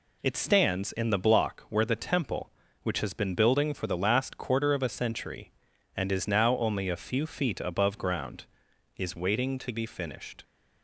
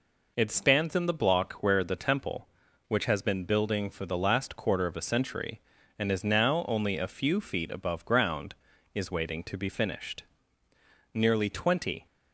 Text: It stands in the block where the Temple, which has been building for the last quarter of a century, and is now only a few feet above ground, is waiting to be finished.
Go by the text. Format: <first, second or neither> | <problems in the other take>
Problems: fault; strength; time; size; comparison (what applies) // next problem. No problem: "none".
first | goes on to say "Nearly twenty"; noticeable; from 11.1 s on; 0.92 s long